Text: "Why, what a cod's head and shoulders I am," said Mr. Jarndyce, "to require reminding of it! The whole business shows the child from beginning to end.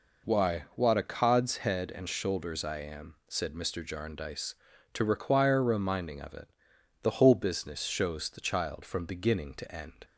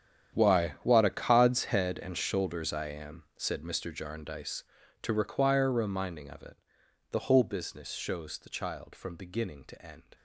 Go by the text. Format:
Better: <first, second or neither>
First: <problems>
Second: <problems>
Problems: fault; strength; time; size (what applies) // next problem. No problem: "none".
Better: first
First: none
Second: gets quieter; strong; throughout; 17 dB